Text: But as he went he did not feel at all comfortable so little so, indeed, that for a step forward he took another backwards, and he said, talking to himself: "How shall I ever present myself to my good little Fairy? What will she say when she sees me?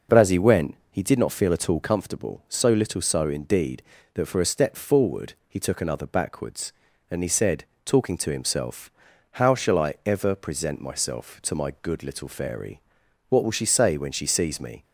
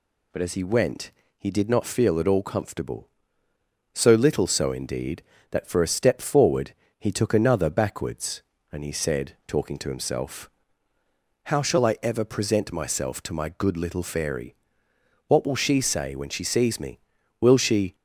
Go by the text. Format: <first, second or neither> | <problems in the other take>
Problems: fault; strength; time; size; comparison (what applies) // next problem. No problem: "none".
first | pauses between "went" and "he"; slight; at 1.1 s; 0.30 s long; slight in the first // pauses between "forward" and "he"; slight; at 6.7 s; 0.30 s long // goes on to say "Will she"; from 17.4 s on; 0.54 s long